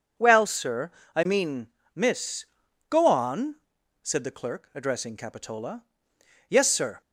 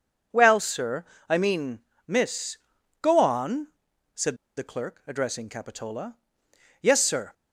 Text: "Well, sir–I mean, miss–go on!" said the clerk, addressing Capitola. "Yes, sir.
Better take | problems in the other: first | pauses between "said" and "the"; slight; at 4.3 s; 0.22 s long

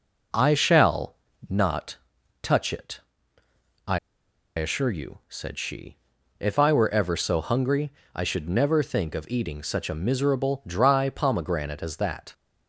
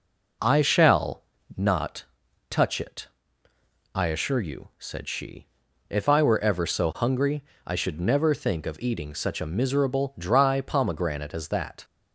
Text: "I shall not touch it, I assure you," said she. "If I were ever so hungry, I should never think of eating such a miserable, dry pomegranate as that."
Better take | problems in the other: second | pauses between "shall" and "not"; slight; at 1.1 s; 0.32 s long; slight in the second // pauses between "not" and "touch"; at 1.9 s; 0.44 s long; also in the second // pauses between "I" and "assure"; noticeable; at 3.9 s; 0.58 s long

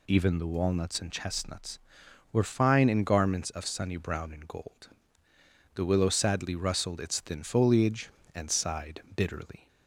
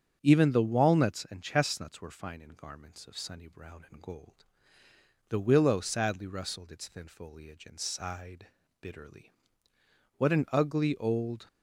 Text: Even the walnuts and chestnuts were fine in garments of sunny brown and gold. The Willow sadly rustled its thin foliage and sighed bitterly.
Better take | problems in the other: first | starts louder than the rest; strong; until 1.2 s; 8 dB // pauses between "sighed" and "bitterly"; slight; at 8.4 s; 0.34 s long // goes on to say "What an ugly old"; noticeable; from 10.1 s on; 1.3 s long

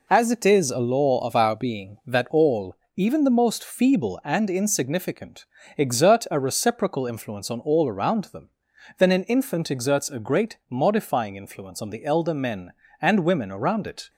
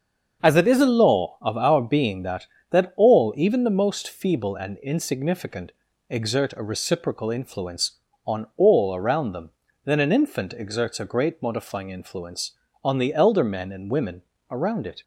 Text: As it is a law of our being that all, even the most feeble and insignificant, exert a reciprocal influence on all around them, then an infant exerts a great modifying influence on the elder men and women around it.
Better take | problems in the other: first | starts louder than the rest; until 1.4 s; 6.5 dB // says "that" twice; at 2.7 s // pauses between "women" and "around"; slight; at 14.2 s; 0.28 s long

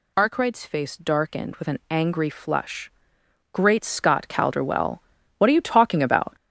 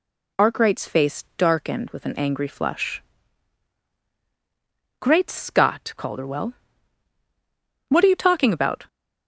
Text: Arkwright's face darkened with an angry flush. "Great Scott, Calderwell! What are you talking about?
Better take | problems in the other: second | gets louder; strong; throughout; 7 dB

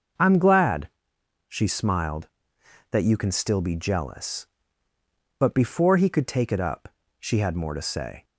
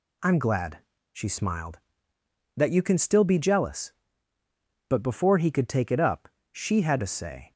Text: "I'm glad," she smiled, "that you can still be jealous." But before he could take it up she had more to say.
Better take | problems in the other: first | pauses between "up" and "she"; slight; at 6.2 s; 0.24 s long; slight in the first // skips "more"; at 6.9 s

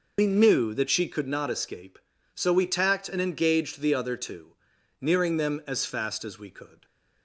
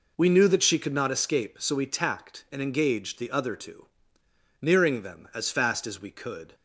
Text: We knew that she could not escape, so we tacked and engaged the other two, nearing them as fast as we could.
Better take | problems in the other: second | loses the start of "We"; at 0.1 s; 80 ms

